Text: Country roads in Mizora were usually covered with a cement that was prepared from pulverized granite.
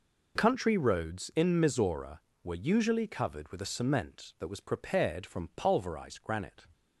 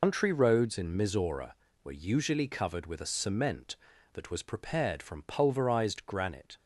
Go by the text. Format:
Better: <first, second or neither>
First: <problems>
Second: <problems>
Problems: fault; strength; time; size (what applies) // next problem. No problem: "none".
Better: first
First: none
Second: loses the start of "Country"; at 0.0 s; 140 ms